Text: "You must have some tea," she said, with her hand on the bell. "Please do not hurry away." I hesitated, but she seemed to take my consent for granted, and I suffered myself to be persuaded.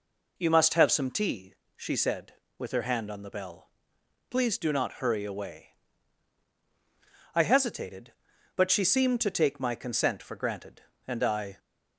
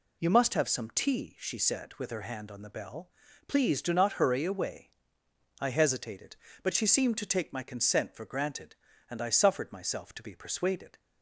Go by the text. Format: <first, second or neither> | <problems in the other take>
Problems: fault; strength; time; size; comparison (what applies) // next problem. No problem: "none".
second | stops before "suffered myself to be persuaded"; at 11.5 s